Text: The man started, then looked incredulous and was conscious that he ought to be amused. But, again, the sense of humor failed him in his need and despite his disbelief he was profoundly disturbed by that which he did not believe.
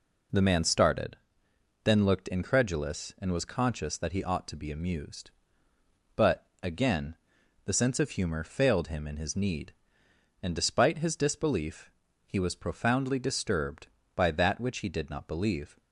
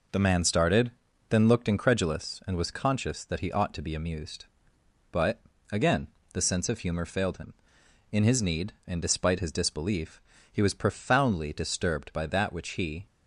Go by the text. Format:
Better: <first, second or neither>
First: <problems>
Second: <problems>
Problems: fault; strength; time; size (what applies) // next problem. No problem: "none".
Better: first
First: pauses between "disbelief" and "he"; slight; at 11.9 s; 0.34 s long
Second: pauses between "disbelief" and "he"; slight; at 10.1 s; 0.32 s long // stops before "did not believe"; at 13.0 s